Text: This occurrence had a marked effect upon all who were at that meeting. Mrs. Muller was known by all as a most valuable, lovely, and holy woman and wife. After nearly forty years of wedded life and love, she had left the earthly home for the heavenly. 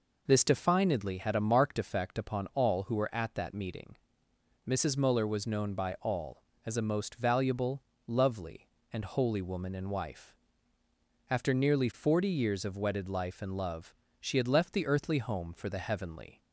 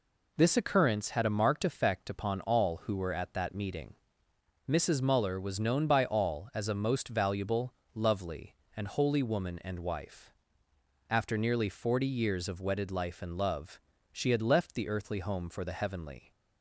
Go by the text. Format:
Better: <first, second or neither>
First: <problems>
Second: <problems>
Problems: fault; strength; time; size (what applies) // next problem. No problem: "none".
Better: second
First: says "definedly" for "occurrence"; at 0.4 s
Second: none